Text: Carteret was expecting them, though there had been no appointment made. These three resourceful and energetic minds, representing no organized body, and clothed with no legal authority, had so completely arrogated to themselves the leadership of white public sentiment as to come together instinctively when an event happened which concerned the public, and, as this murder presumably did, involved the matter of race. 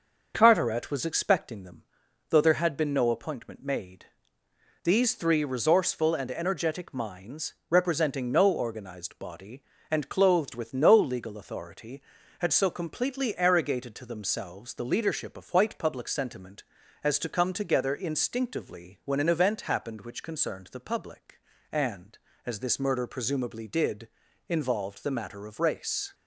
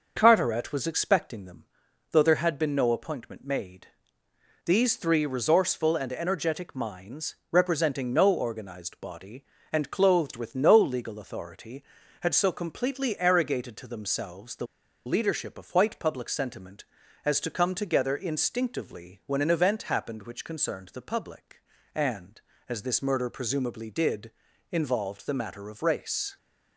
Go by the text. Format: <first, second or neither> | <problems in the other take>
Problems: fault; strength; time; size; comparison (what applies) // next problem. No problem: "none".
first | starts louder than the rest; noticeable; until 1.1 s; 6 dB; noticeable in the first // pauses between "the" and "leadership"; at 14.6 s; 0.40 s long